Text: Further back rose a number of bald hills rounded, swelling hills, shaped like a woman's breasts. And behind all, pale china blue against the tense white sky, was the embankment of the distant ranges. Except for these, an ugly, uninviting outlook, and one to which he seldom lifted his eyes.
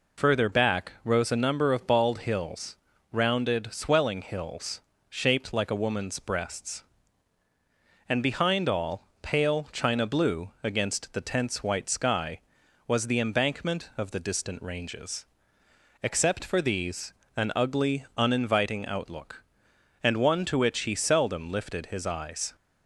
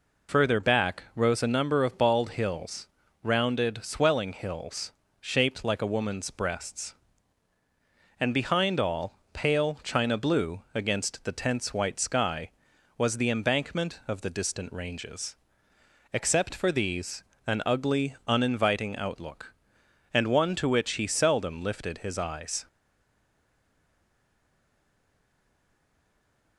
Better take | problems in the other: first | pauses between "hills" and "rounded"; at 2.8 s; 0.38 s long; also in the first // stays silent after the last word; strong; from 22.6 s on; 3.9 s long

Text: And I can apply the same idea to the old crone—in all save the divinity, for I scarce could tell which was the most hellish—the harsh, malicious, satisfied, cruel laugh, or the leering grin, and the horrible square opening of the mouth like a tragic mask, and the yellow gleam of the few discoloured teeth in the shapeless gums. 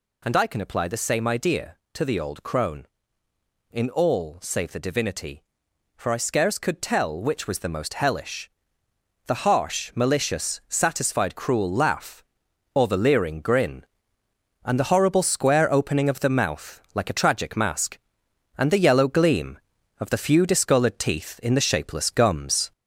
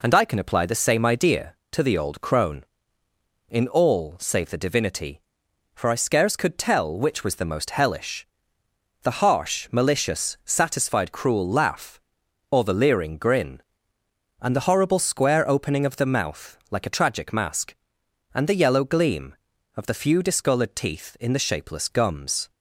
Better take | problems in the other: second | gets louder; slight; throughout; 3 dB

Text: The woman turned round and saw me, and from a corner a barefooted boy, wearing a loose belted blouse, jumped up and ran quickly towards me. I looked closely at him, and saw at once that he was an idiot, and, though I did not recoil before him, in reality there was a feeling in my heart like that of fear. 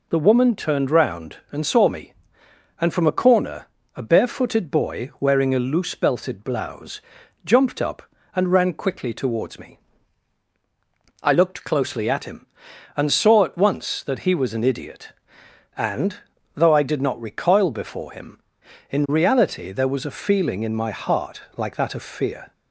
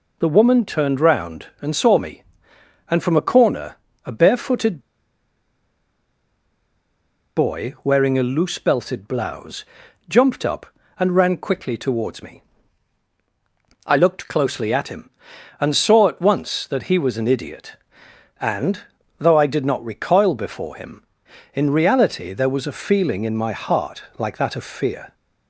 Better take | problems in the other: first | pauses between "corner" and "a"; slight; at 3.7 s; 0.30 s long; slight in the first // pauses between "barefooted" and "boy"; strong; at 4.7 s; 2.5 s long // pauses between "heart" and "like"; slight; at 24.0 s; 0.16 s long; slight in the first

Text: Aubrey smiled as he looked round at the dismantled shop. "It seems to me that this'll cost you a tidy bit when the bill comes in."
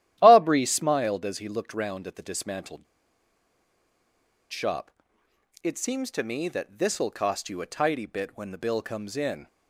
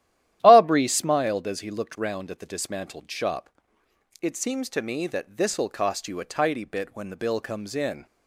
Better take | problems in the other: second | starts louder than the rest; strong; until 1.2 s; 12.5 dB; strong in the second // pauses between "dismantled" and "shop"; strong; at 2.8 s; 1.6 s long

